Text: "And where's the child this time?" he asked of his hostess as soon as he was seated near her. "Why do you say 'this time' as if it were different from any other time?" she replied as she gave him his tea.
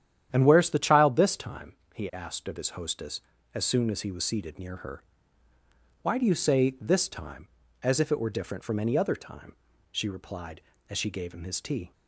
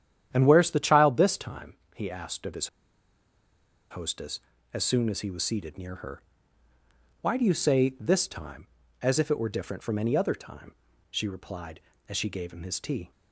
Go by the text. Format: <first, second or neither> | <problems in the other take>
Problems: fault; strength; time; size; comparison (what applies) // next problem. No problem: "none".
first | starts louder than the rest; strong; until 1.3 s; 10 dB; strong in the first // pauses between "his" and "hostess"; at 2.6 s; 1.2 s long